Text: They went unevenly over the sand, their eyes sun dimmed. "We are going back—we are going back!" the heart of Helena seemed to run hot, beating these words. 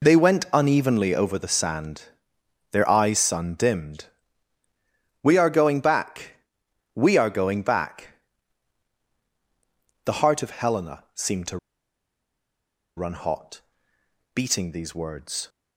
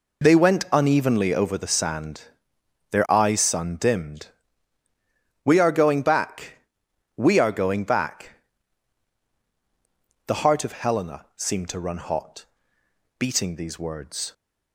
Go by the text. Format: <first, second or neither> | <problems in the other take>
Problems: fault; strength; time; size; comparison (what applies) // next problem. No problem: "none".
second | pauses between "to" and "run"; strong; at 11.5 s; 1.3 s long